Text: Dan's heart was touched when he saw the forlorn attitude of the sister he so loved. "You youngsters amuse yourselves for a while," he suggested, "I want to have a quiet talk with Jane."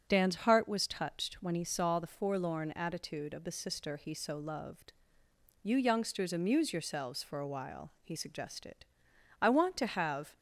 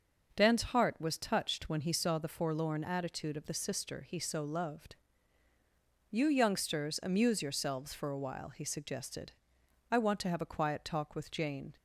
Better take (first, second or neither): second